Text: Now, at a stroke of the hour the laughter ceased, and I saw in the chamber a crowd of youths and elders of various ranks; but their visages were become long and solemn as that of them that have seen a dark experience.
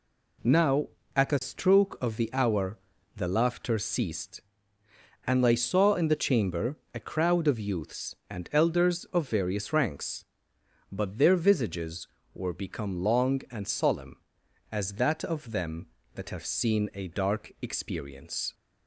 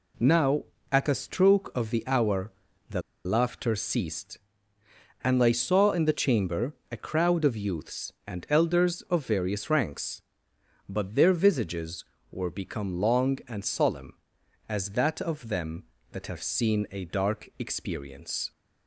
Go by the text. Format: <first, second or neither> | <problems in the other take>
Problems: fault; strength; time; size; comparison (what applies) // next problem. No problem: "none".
first | pauses between "hour" and "the"; at 2.5 s; 0.38 s long; also in the first // pauses between "the" and "laughter"; slight; at 3.0 s; 0.23 s long // pauses between "chamber" and "a"; slight; at 6.7 s; 0.20 s long; slight in the first